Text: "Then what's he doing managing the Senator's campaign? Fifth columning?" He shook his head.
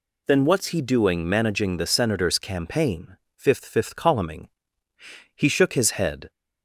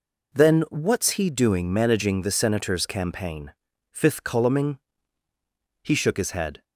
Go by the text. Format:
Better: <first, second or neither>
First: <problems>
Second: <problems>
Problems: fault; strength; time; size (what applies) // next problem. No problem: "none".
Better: second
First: says "Fifth" twice; at 3.6 s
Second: none